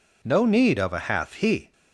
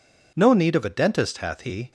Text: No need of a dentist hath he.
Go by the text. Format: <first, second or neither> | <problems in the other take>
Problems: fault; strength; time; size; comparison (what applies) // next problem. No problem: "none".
second | skips "dentist"; at 0.9 s